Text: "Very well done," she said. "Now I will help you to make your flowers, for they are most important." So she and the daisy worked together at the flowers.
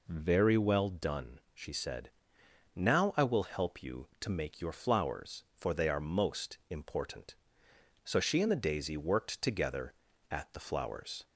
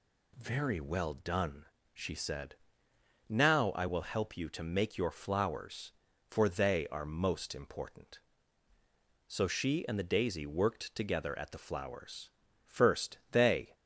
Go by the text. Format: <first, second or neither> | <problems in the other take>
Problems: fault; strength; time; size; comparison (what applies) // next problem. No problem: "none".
first | goes on to say "First they"; noticeable; from 12.6 s on; 1.1 s long